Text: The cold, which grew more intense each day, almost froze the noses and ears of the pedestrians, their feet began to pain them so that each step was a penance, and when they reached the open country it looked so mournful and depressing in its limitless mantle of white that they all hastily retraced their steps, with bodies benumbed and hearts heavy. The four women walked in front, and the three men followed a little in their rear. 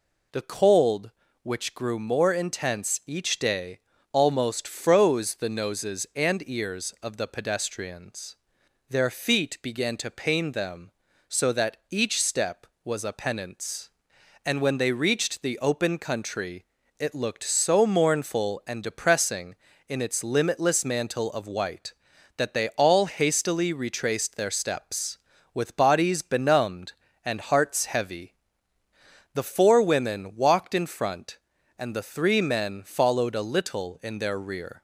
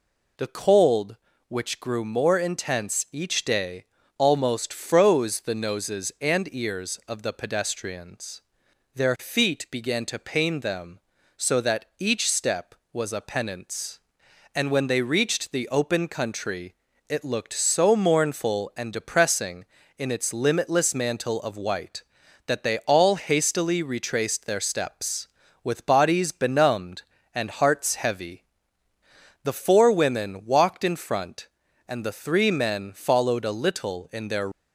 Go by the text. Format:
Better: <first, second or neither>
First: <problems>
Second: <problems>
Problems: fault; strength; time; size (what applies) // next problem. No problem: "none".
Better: first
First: pauses between "country" and "it"; slight; at 16.6 s; 0.36 s long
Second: pauses between "country" and "it"; slight; at 16.7 s; 0.36 s long // stops before "rear"; at 34.5 s